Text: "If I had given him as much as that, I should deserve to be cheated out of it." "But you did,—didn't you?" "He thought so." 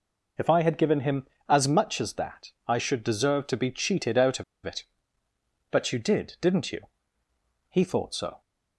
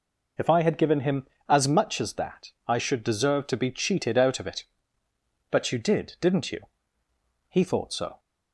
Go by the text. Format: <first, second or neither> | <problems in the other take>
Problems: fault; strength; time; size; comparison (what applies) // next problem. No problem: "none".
second | pauses between "of" and "it"; slight; at 4.4 s; 0.22 s long